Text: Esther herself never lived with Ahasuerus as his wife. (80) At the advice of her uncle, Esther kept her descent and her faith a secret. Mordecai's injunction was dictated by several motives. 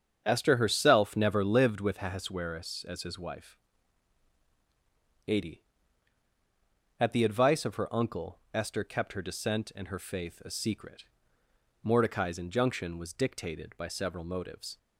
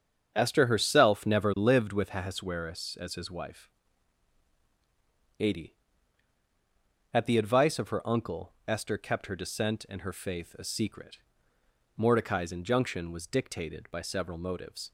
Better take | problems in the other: neither | starts louder than the rest; strong; the same in both

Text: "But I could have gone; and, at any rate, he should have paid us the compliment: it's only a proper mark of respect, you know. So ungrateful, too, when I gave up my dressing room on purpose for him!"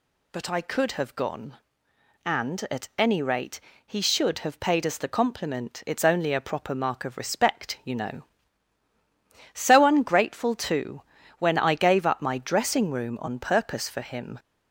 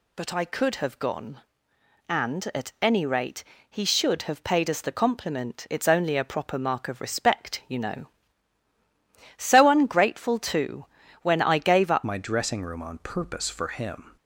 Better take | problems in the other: first | changes voice at "my"; from 12.0 s on; 2.1 s long

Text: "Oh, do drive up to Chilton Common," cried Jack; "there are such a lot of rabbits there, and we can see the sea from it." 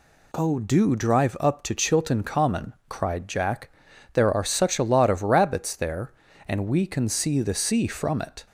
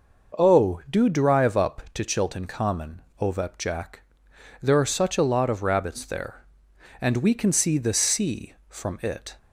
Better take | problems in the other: first | says "ovep" for "cried"; at 3.2 s

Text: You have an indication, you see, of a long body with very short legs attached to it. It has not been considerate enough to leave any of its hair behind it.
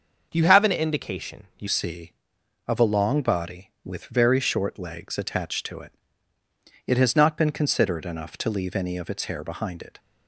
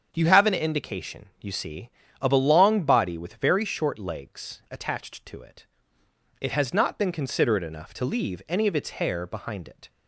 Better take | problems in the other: second | starts louder than the rest; until 1.3 s; 6.5 dB; strong in the second // changes voice at "see"; from 1.6 s on; 8.3 s long

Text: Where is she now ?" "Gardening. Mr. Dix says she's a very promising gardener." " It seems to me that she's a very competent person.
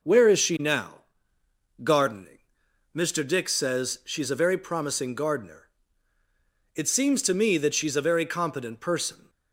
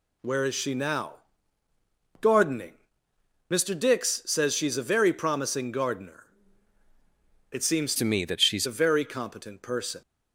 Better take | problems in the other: first | changes voice from "to" to "she's"; from 7.9 to 8.6 s; 0.7 s long

